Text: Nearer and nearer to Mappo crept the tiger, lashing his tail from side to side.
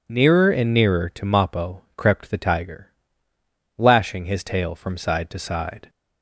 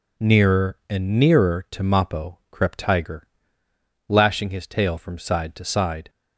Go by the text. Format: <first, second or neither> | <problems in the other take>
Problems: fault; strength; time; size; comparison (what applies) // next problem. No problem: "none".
first | skips "the"; at 2.7 s